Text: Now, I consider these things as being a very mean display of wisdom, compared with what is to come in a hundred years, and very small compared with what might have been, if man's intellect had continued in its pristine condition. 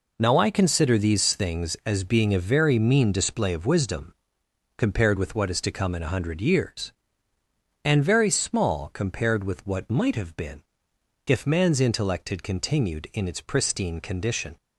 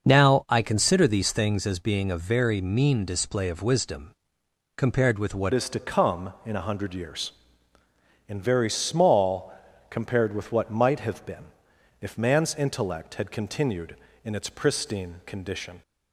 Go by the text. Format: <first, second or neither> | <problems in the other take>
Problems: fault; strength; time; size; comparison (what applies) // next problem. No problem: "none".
first | starts louder than the rest; noticeable; until 1.1 s; 6 dB // changes voice at "is"; from 5.5 s on; 10.3 s long // pauses between "small" and "compared"; slight; at 9.5 s; 0.34 s long